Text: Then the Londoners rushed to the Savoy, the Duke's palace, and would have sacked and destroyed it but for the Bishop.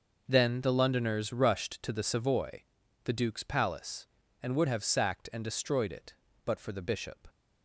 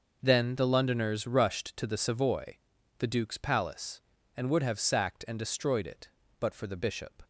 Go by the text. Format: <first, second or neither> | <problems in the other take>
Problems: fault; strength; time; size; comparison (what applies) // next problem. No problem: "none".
neither | none